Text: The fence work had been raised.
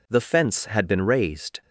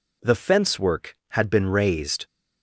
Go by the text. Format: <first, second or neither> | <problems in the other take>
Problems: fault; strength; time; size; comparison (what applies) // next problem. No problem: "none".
second | skips "work"; at 0.6 s